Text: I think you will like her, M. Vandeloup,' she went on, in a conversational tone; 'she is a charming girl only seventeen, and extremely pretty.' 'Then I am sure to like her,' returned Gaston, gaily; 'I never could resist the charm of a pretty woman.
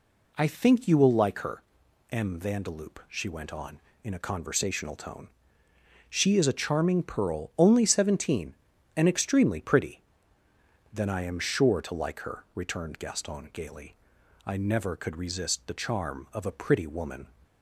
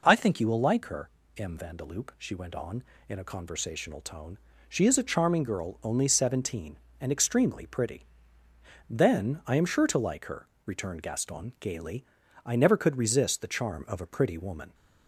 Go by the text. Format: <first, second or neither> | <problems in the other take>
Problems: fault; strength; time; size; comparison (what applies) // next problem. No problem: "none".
second | says "pearl" for "girl"; at 7.0 s